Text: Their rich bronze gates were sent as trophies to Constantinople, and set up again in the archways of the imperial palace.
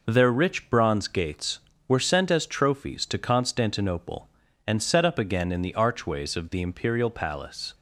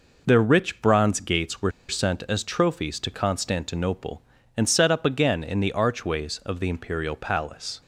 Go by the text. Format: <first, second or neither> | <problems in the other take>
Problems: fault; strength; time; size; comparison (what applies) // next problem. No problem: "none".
first | pauses between "were" and "sent"; slight; at 1.7 s; 0.17 s long